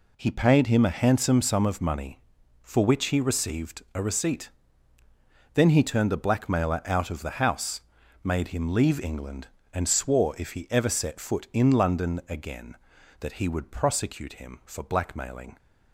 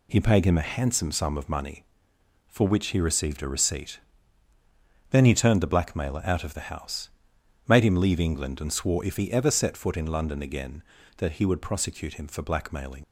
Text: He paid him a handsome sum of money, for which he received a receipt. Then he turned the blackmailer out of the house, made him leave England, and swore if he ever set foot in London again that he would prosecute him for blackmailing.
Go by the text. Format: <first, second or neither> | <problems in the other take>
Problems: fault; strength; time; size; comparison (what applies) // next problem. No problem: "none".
first | leaves "blackmailing" unfinished; at 13.0 s; 65 ms